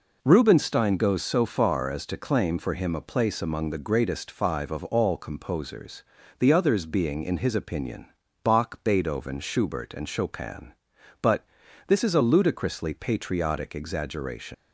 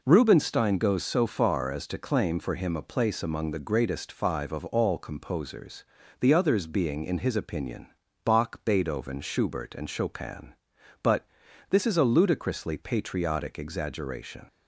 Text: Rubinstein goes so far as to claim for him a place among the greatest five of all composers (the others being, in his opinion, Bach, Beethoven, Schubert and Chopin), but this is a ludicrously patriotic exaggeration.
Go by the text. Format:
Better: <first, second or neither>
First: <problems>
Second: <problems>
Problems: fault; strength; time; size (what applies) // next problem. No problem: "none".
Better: second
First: pauses between "but" and "this"; at 11.4 s; 0.40 s long // leaves "exaggeration" unfinished; at 14.5 s; 85 ms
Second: pauses between "but" and "this"; at 11.2 s; 0.41 s long